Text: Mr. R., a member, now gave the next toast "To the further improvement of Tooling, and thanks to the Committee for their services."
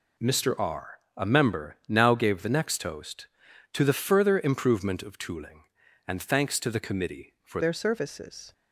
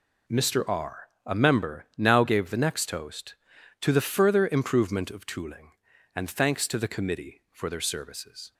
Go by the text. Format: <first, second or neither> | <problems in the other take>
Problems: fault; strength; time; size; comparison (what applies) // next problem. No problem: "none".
second | changes voice at "their"; from 7.6 s on; 0.9 s long